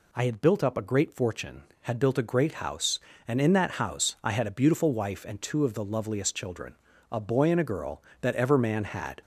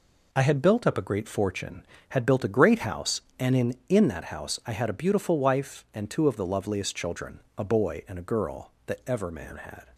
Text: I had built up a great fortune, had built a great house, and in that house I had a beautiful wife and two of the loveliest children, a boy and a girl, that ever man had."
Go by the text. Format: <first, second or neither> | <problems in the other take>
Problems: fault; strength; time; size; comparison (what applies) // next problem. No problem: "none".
first | says "in" twice; at 3.8 s